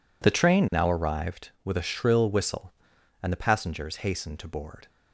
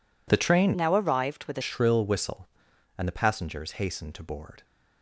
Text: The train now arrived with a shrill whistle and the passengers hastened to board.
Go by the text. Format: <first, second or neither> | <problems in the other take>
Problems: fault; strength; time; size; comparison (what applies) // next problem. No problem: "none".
first | changes voice from "now" to "a"; from 0.7 to 1.6 s; 0.9 s long